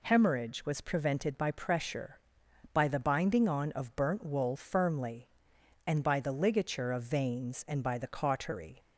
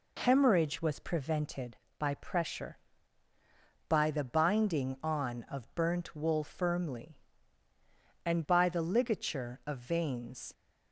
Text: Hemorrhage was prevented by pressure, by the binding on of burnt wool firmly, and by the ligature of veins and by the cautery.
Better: first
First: none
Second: stops before "and by the cautery"; at 10.5 s

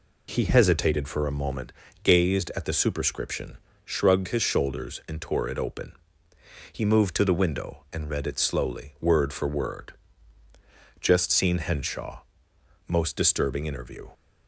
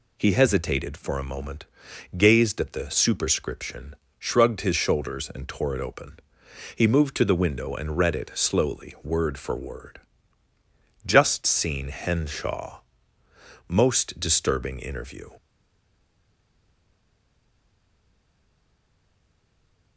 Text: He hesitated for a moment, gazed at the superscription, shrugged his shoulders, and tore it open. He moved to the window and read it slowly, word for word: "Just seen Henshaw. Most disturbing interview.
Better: first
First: none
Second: stays silent after the last word; strong; from 15.3 s on; 4.6 s long

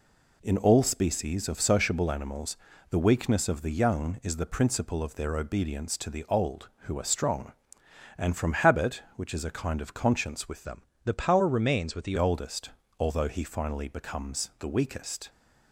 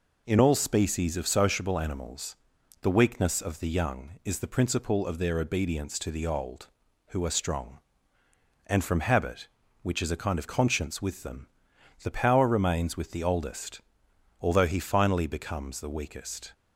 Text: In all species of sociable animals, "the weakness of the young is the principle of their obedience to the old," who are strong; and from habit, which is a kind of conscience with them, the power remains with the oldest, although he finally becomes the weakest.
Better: second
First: changes voice from "them" to "the"; from 10.6 to 12.1 s; 1.5 s long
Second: none

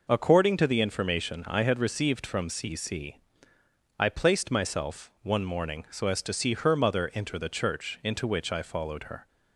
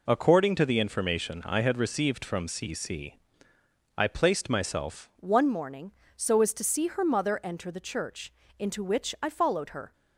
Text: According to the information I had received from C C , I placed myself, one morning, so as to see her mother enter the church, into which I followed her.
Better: first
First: none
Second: changes voice at "one"; from 5.1 s on; 4.8 s long

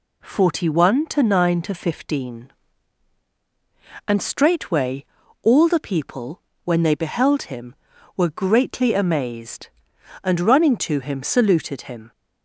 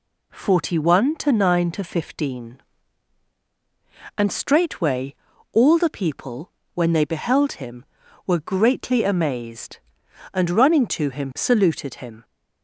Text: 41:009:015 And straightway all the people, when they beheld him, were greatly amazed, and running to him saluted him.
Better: neither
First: pauses between "straightway" and "all"; at 5.0 s; 0.38 s long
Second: pauses between "straightway" and "all"; at 5.1 s; 0.38 s long

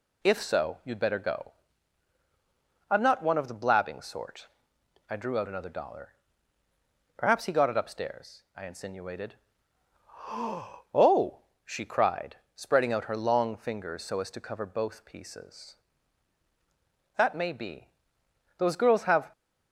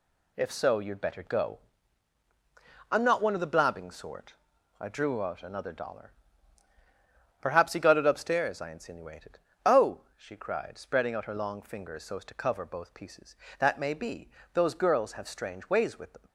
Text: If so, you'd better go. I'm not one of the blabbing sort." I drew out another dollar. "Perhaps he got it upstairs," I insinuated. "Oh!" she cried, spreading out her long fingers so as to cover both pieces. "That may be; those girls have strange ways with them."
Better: second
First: stops before "strange ways with them"; at 19.3 s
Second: none

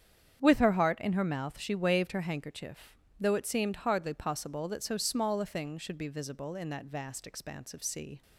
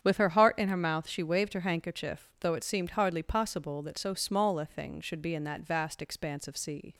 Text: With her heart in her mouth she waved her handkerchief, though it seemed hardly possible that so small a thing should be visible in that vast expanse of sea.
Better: first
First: starts louder than the rest; strong; until 1.4 s; 8.5 dB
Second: starts louder than the rest; strong; until 1.0 s; 8.5 dB // skips "visible"; at 5.3 s

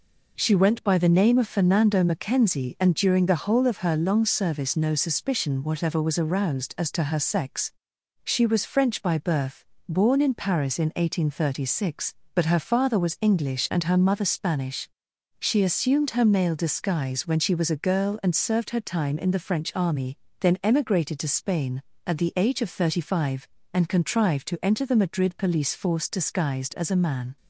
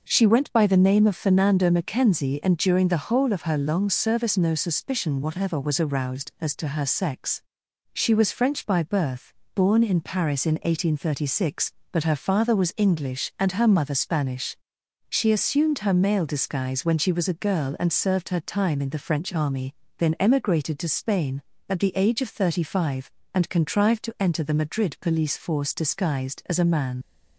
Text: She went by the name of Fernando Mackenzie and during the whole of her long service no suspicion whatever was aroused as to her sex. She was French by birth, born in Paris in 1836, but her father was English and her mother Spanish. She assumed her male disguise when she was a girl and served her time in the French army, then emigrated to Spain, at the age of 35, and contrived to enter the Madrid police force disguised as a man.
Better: first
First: none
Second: leaves "man" unfinished; at 27.0 s; 55 ms

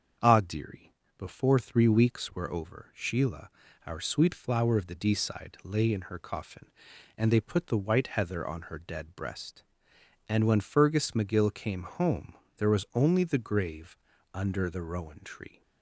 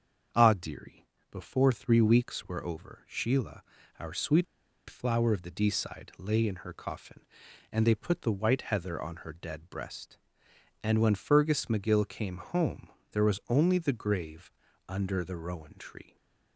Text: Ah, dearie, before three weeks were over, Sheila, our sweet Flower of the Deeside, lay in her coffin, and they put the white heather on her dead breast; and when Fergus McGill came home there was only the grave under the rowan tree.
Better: first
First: starts louder than the rest; until 1.4 s; 7 dB // pauses between "home" and "there"; slight; at 12.3 s; 0.24 s long // pauses between "grave" and "under"; at 13.9 s; 0.38 s long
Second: starts louder than the rest; until 1.6 s; 7 dB // pauses between "sweet" and "Flower"; at 4.4 s; 0.44 s long // pauses between "home" and "there"; slight; at 12.8 s; 0.24 s long // pauses between "grave" and "under"; at 14.4 s; 0.38 s long

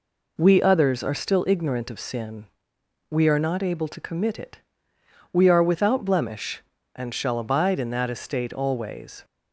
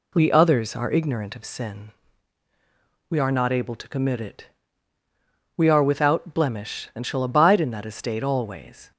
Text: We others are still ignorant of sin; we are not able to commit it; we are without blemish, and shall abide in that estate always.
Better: first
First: none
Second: skips "still"; at 0.9 s

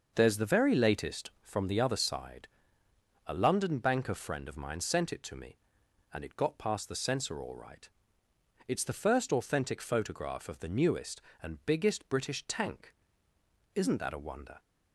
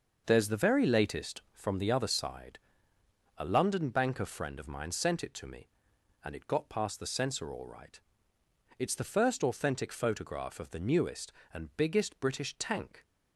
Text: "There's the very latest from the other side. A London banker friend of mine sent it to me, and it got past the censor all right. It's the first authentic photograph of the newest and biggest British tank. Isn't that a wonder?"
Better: first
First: starts louder than the rest; noticeable; until 1.1 s; 6 dB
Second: starts louder than the rest; noticeable; until 1.2 s; 6 dB // stops before "Isn't that a wonder"; at 13.0 s

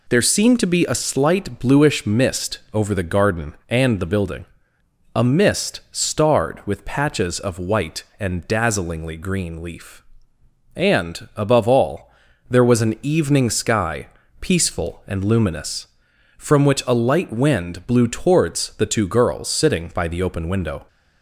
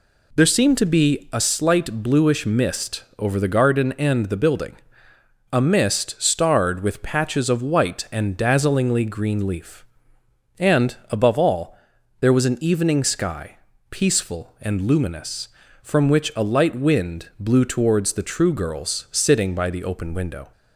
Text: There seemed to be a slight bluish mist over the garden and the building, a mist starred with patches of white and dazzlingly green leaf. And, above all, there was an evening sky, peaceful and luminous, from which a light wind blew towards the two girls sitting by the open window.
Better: first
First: none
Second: says "true" for "two"; at 18.2 s

